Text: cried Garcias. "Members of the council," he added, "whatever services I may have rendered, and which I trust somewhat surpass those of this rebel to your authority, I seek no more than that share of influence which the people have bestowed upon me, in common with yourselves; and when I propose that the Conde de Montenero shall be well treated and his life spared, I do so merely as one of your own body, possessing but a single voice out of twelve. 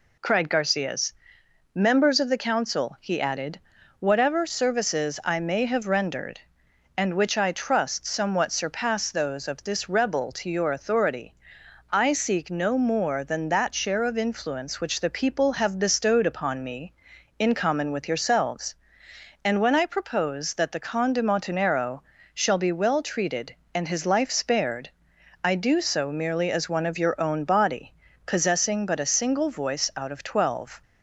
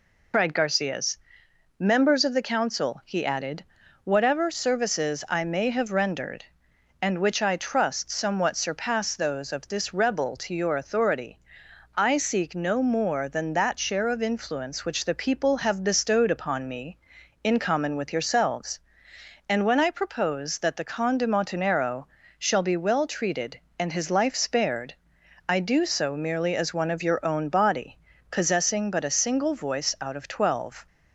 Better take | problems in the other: first | loses the start of "cried"; at 0.3 s; 95 ms // pauses between "Montenero" and "shall"; slight; at 22.0 s; 0.32 s long; slight in the first

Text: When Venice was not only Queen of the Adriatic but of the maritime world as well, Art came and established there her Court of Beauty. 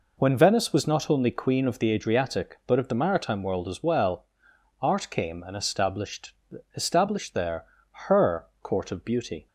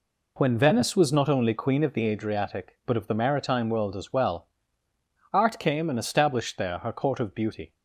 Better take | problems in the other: second | says "established" twice; at 6.7 s // pauses between "there" and "her"; at 7.6 s; 0.44 s long

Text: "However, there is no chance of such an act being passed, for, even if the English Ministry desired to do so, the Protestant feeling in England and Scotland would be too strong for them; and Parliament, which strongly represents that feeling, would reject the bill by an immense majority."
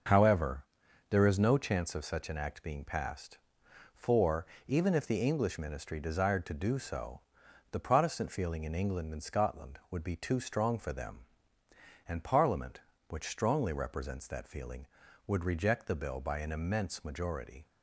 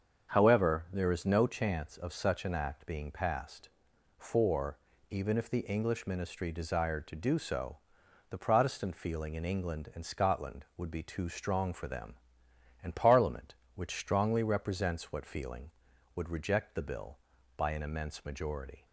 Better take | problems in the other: first | starts louder than the rest; until 1.3 s; 7 dB // says "what" for "that"; at 15.1 s

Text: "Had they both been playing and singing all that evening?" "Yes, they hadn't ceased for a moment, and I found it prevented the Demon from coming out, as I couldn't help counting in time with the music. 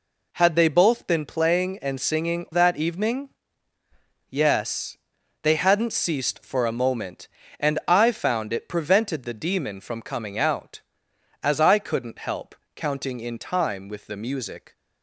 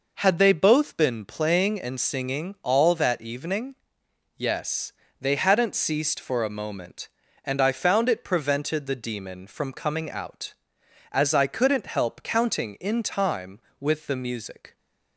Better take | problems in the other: second | skips "all"; at 2.4 s // pauses between "help" and "counting"; slight; at 12.5 s; 0.18 s long

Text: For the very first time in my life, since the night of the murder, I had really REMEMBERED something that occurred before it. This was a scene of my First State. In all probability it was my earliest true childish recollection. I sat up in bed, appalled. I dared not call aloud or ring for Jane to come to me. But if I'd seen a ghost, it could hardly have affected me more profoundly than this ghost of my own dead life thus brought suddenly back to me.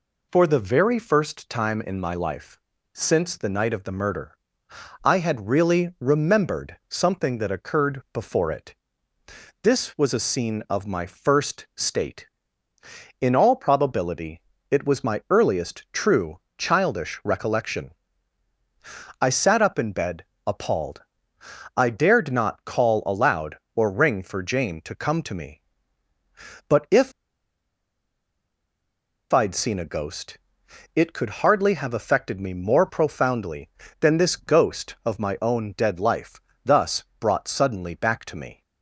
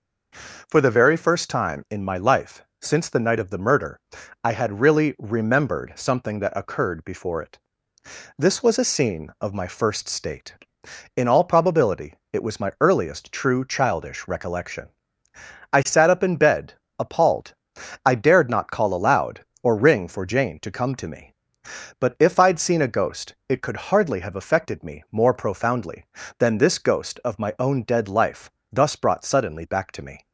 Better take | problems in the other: second | pauses between "probability" and "it"; slight; at 14.3 s; 0.30 s long; slight in the second // pauses between "true" and "childish"; slight; at 16.3 s; 0.20 s long // pauses between "if" and "I'd"; strong; at 27.1 s; 2.2 s long // pauses between "life" and "thus"; slight; at 36.4 s; 0.24 s long; slight in the second // pauses between "thus" and "brought"; slight; at 37.0 s; 0.20 s long

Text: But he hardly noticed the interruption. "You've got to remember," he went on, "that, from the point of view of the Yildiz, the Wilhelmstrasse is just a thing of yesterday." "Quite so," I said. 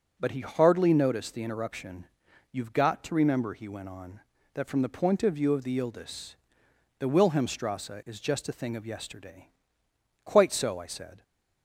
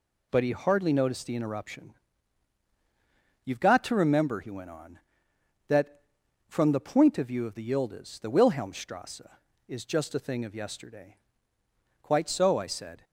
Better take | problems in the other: neither | none

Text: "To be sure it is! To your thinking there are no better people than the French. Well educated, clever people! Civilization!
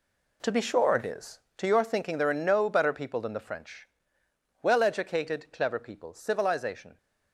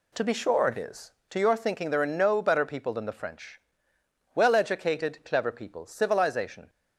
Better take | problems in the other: second | gets quieter; strong; throughout; 11.5 dB

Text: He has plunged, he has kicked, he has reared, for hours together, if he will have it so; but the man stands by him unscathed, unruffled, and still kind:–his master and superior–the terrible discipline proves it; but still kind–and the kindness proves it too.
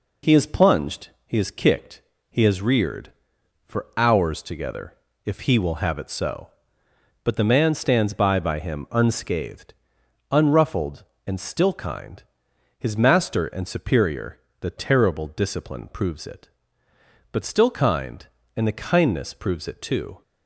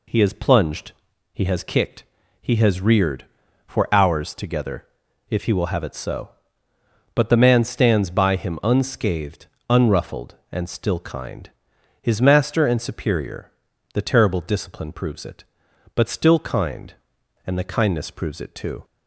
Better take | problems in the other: second | says "by" twice; at 8.4 s

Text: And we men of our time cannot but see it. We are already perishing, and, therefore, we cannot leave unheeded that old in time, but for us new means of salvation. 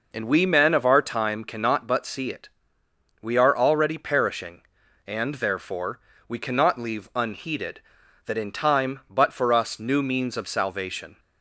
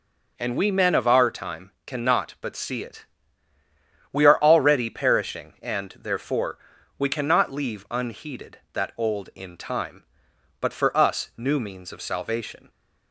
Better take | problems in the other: second | skips "old"; at 8.3 s

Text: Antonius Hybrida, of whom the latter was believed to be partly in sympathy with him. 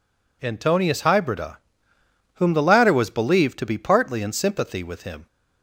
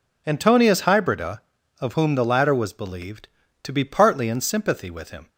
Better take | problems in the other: second | skips "of"; at 1.9 s

